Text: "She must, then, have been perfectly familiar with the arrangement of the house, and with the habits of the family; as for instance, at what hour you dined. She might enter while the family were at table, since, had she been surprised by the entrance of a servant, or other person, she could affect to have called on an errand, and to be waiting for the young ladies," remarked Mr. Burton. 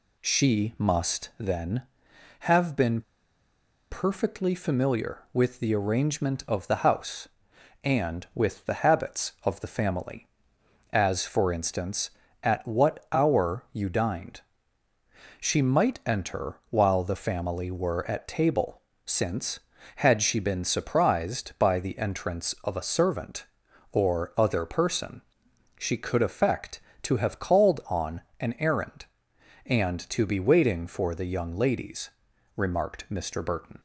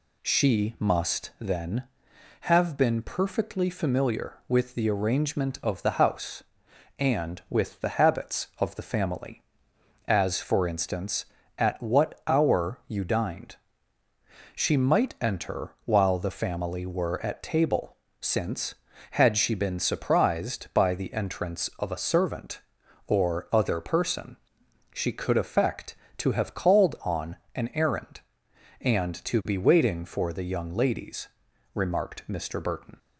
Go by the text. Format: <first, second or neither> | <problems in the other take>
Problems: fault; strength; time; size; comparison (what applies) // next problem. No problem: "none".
second | pauses between "been" and "perfectly"; noticeable; at 3.0 s; 0.88 s long // pauses between "on" and "an"; slight; at 28.2 s; 0.18 s long; slight in the second